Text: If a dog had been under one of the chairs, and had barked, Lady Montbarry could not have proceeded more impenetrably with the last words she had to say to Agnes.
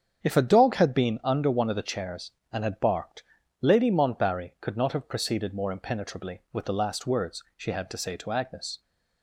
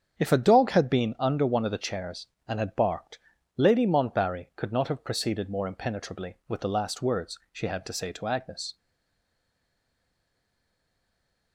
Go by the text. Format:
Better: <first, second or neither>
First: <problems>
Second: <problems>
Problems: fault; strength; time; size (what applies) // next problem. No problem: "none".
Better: first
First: starts louder than the rest; strong; until 1.2 s; 7.5 dB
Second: starts louder than the rest; strong; until 1.2 s; 7.5 dB // stays silent after the last word; strong; from 8.7 s on; 2.8 s long